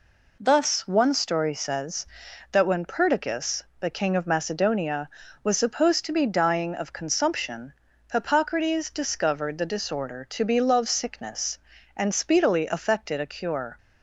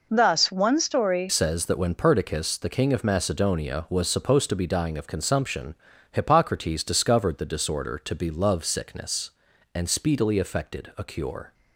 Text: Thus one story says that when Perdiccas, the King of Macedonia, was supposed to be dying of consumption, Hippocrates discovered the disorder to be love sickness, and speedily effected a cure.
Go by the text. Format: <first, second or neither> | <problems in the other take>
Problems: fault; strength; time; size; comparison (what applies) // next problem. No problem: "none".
first | changes voice at "says"; from 1.2 s on; 10.3 s long